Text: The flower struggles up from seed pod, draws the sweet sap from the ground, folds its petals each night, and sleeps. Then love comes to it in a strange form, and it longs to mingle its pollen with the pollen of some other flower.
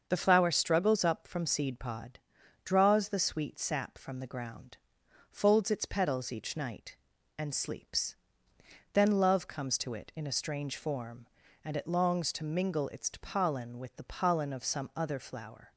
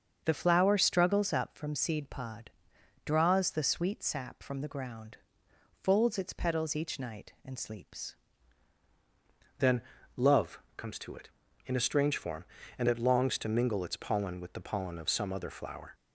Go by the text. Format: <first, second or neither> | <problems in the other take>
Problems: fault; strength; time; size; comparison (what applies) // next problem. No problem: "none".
first | starts louder than the rest; until 1.2 s; 6.5 dB; also in the first // changes voice at "Then"; from 9.5 s on; 6.4 s long // pauses between "Then" and "love"; slight; at 9.8 s; 0.36 s long // pauses between "love" and "comes"; slight; at 10.5 s; 0.18 s long